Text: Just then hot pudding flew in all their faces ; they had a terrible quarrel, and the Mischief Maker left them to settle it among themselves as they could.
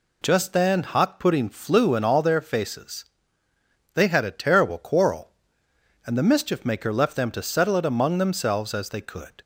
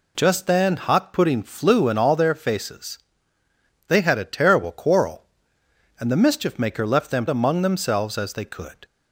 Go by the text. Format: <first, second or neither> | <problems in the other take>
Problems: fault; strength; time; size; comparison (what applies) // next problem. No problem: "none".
first | skips "to settle it"; at 7.2 s